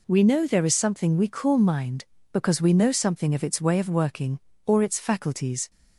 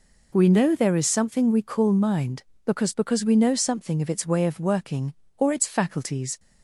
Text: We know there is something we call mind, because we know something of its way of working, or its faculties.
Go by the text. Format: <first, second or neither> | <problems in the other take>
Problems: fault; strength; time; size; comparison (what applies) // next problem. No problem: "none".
first | says "because" twice; at 2.9 s